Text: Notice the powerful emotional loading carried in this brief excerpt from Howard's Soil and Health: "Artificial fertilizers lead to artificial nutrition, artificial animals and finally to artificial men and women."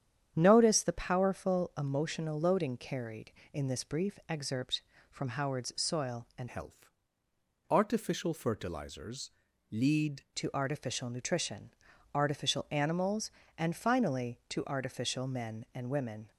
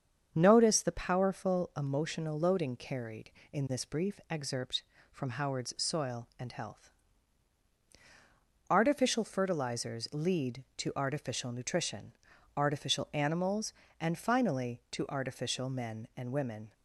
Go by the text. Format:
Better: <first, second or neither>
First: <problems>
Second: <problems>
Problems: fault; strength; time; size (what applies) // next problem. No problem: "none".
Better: second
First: starts louder than the rest; strong; until 1.3 s; 9 dB // changes voice from "Health" to "lead"; from 6.4 to 10.2 s; 3.8 s long // pauses between "fertilizers" and "lead"; at 9.2 s; 0.42 s long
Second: starts louder than the rest; strong; until 1.3 s; 7.5 dB